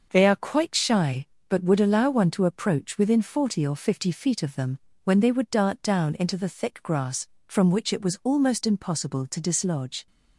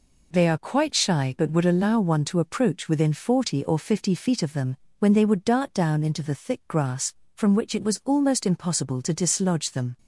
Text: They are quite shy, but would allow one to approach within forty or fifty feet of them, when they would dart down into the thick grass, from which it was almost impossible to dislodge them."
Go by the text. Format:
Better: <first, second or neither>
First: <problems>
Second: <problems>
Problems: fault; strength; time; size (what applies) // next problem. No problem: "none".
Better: second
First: starts louder than the rest; noticeable; until 1.1 s; 6 dB // stops before "them"; at 10.0 s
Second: none